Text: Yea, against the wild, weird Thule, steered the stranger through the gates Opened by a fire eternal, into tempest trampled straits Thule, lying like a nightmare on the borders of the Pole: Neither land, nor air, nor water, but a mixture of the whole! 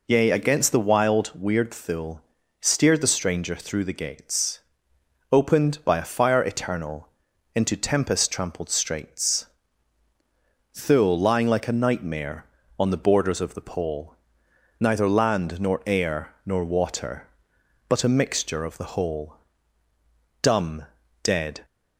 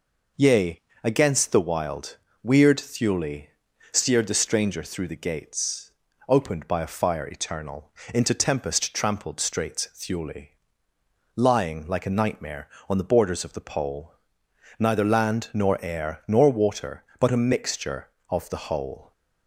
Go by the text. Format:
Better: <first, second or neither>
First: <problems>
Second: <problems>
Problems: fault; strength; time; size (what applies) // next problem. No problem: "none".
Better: second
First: pauses between "gates" and "Opened"; noticeable; at 4.5 s; 0.72 s long // pauses between "straits" and "Thule"; strong; at 9.4 s; 1.2 s long // goes on to say "Dumb dead"; noticeable; from 20.4 s on; 1.2 s long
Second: pauses between "gates" and "Opened"; slight; at 5.9 s; 0.36 s long